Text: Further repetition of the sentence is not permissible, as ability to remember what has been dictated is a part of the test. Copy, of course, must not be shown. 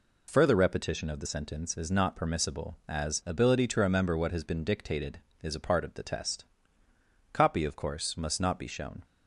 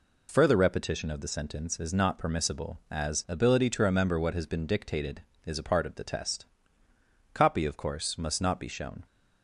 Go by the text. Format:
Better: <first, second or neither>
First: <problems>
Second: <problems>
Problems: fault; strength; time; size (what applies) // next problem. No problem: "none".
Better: neither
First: none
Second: none